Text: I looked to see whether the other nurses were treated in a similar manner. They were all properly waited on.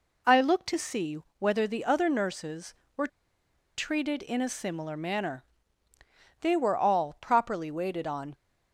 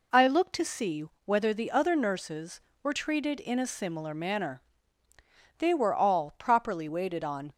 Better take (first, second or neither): second